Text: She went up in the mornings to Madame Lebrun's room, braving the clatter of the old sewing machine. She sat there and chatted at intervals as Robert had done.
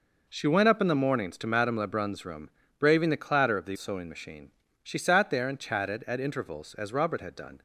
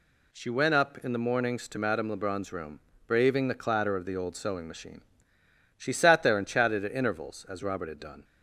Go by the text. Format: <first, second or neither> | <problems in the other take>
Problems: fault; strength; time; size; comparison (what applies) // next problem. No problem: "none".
second | skips "old"; at 3.7 s